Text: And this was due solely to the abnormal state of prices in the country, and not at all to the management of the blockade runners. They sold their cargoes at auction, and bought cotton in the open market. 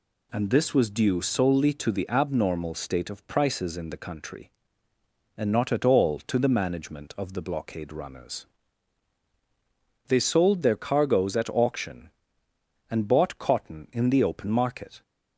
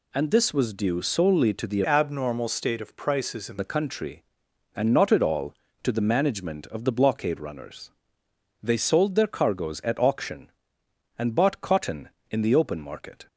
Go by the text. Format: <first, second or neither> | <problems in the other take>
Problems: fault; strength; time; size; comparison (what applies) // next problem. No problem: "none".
first | changes voice from "abnormal" to "in"; from 1.8 to 3.5 s; 1.7 s long